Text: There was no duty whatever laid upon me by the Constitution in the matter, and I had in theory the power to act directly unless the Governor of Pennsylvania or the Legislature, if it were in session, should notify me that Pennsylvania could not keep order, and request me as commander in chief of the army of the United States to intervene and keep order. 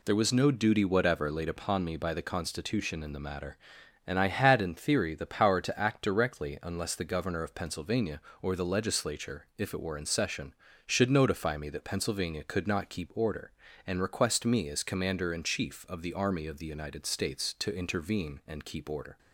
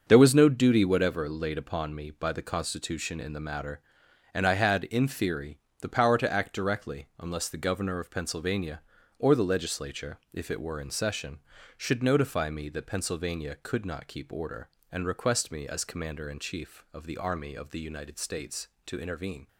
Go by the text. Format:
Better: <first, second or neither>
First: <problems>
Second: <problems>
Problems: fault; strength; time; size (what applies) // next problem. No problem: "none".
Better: first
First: none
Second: starts louder than the rest; until 1.0 s; 6.5 dB // pauses between "theory" and "the"; slight; at 5.5 s; 0.22 s long // stops before "and keep order"; at 19.4 s